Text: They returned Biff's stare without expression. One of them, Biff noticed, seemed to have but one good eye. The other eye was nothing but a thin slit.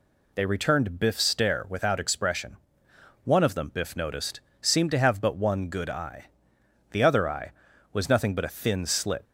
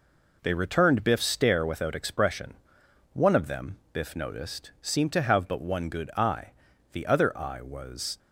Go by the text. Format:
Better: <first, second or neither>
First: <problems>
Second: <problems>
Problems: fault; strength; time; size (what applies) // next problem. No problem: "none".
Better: first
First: none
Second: stops before "nothing but a thin slit"; at 8.1 s